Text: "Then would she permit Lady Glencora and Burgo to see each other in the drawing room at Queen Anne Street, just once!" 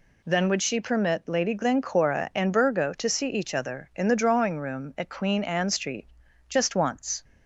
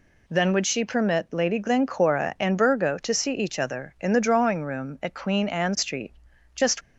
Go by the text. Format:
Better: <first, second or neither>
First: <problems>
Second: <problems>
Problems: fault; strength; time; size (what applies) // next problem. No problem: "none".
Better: first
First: none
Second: stops before "once"; at 6.8 s